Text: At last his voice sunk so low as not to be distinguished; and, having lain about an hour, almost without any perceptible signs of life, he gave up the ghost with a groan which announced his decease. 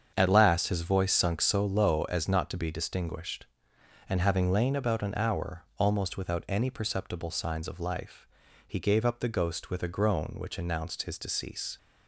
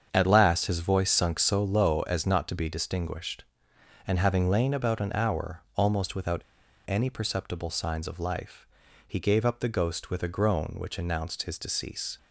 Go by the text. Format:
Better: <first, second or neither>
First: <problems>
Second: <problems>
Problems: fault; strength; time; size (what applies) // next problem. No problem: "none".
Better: first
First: starts louder than the rest; strong; until 1.1 s; 7.5 dB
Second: starts louder than the rest; strong; until 1.1 s; 7.5 dB // pauses between "without" and "any"; noticeable; at 6.4 s; 0.47 s long